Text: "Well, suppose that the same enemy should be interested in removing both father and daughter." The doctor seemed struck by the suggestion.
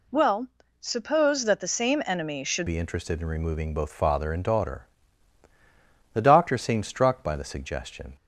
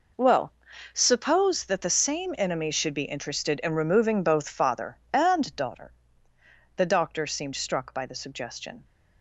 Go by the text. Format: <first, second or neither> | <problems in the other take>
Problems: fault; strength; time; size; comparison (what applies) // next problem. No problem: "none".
second | changes voice at "be"; from 2.6 s on; 5.5 s long